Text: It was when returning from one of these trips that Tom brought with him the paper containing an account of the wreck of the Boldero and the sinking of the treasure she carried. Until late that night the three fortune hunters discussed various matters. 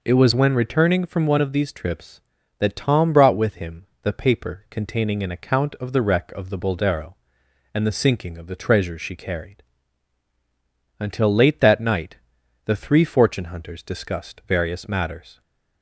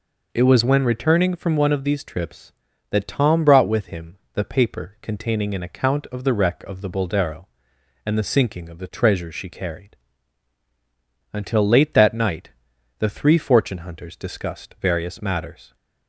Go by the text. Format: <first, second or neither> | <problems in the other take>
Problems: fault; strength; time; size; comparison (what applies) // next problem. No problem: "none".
neither | pauses between "him" and "the"; slight; the same in both // pauses between "night" and "the"; noticeable; the same in both